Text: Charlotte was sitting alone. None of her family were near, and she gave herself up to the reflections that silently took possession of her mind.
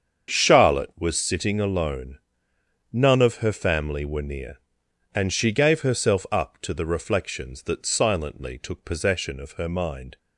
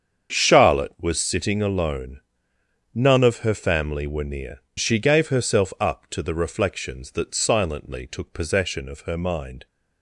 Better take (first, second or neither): first